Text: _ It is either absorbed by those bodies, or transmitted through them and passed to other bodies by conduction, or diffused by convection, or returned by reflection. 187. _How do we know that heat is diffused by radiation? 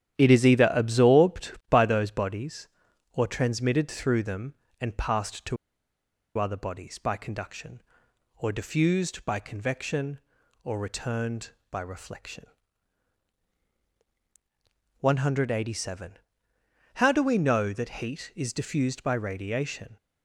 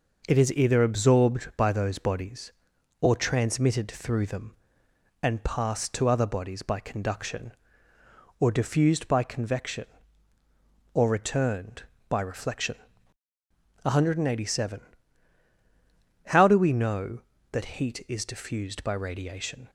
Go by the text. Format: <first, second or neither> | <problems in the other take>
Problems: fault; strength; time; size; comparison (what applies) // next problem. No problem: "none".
second | starts louder than the rest; strong; until 1.2 s; 11 dB // pauses between "to" and "other"; noticeable; at 5.5 s; 0.82 s long